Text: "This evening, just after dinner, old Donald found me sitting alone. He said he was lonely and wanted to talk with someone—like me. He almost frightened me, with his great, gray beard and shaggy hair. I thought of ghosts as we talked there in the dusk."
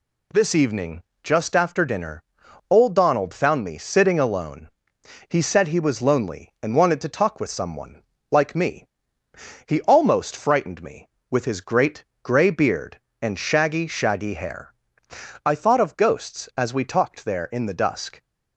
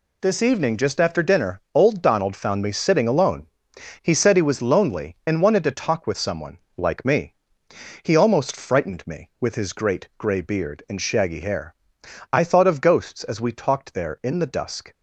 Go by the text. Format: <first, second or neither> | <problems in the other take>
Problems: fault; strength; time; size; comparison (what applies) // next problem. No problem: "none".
second | says "shaggy" twice; at 13.8 s